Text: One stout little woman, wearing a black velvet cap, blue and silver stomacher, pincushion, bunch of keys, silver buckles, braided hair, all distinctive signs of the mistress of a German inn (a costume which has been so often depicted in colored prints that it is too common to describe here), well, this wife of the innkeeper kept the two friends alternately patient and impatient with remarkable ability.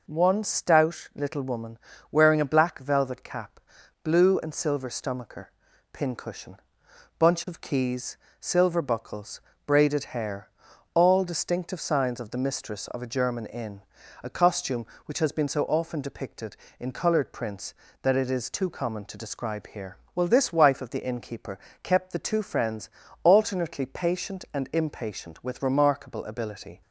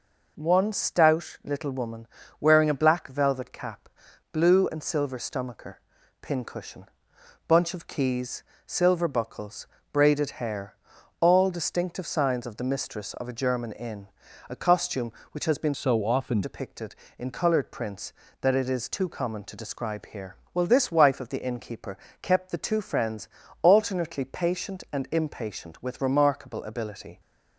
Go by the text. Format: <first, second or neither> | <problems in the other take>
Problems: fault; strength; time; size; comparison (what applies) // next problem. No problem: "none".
first | changes voice from "so" to "often"; from 15.7 to 16.4 s; 0.7 s long // pauses between "innkeeper" and "kept"; slight; at 21.9 s; 0.24 s long; slight in the first // pauses between "friends" and "alternately"; slight; at 23.2 s; 0.34 s long; slight in the first